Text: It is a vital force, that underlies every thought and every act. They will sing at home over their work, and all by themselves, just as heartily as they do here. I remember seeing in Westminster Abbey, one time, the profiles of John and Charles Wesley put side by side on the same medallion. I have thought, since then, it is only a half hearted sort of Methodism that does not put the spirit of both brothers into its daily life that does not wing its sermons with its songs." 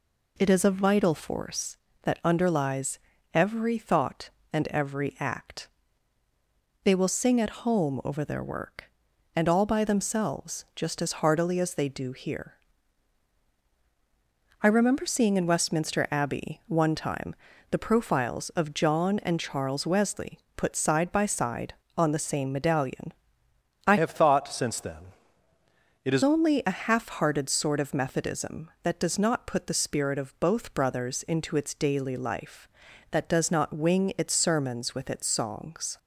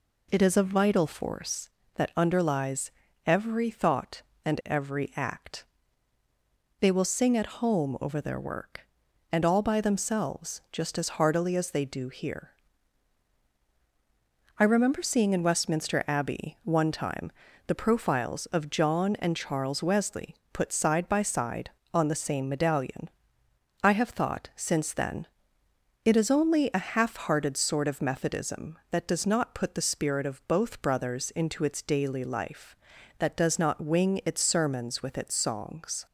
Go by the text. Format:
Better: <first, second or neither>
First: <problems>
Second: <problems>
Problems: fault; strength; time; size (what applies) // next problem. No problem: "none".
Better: second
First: pauses between "underlies" and "every"; slight; at 2.9 s; 0.34 s long // pauses between "Wesley" and "put"; slight; at 20.3 s; 0.16 s long // changes voice from "have" to "is"; from 23.9 to 26.2 s; 2.3 s long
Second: pauses between "underlies" and "every"; slight; at 2.9 s; 0.34 s long // pauses between "Wesley" and "put"; slight; at 20.3 s; 0.16 s long